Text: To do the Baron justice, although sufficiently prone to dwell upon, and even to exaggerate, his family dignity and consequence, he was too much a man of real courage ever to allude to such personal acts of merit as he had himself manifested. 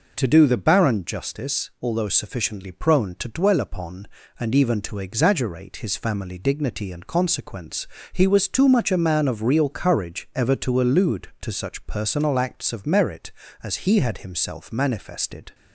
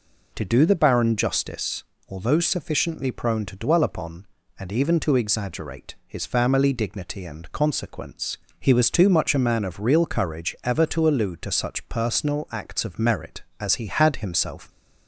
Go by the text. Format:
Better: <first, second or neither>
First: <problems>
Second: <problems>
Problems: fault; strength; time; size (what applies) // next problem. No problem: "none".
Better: first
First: none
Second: stops before "manifested"; at 14.6 s